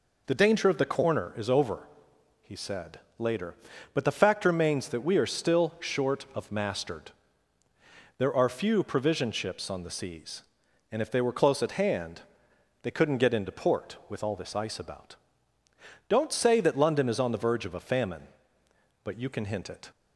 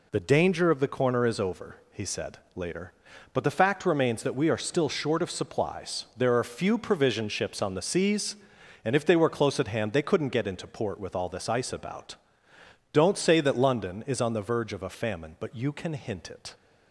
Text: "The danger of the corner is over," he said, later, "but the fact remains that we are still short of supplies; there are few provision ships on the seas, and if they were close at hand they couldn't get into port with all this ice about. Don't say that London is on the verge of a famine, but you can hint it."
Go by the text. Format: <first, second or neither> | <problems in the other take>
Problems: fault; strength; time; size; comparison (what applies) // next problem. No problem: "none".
second | says "mastered" for "supplies"; at 6.5 s // pauses between "hand" and "they"; noticeable; at 12.2 s; 0.60 s long